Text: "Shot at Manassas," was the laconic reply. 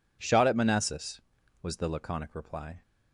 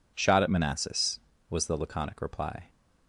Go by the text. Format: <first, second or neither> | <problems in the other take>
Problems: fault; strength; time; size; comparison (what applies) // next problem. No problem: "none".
neither | none